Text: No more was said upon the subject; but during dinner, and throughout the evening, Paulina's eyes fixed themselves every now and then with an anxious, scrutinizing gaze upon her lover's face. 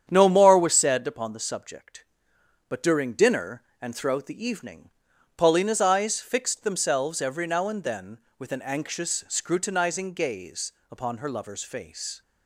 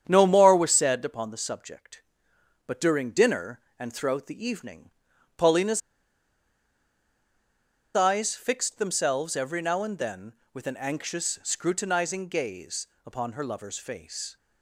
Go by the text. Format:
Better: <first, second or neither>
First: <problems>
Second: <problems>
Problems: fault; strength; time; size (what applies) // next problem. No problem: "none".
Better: first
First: starts louder than the rest; strong; until 1.1 s; 9 dB // pauses between "gaze" and "upon"; slight; at 10.7 s; 0.18 s long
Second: starts louder than the rest; strong; until 1.0 s; 9 dB // pauses between "Paulina's" and "eyes"; strong; at 5.7 s; 2.1 s long // pauses between "gaze" and "upon"; slight; at 12.8 s; 0.18 s long